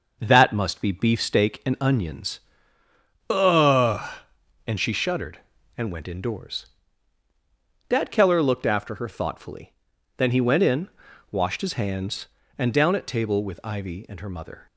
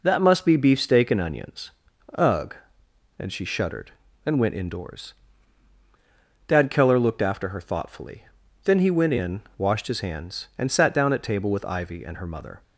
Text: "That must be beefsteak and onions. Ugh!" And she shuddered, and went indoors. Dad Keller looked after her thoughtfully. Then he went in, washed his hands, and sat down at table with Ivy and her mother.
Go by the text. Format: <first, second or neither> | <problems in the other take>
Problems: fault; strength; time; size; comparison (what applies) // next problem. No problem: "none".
second | skips "sat"; at 12.7 s